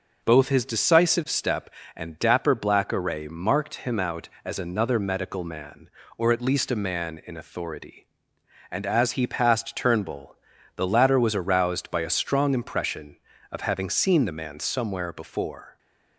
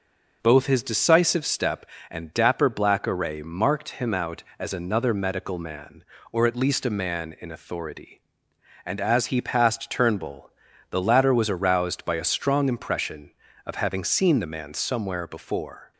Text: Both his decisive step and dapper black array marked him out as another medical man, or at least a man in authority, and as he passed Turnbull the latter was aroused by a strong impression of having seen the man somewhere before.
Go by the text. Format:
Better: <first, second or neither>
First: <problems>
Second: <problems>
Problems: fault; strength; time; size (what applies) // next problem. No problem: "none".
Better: neither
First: pauses between "Turnbull" and "the"; at 10.3 s; 0.40 s long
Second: pauses between "Turnbull" and "the"; at 10.5 s; 0.40 s long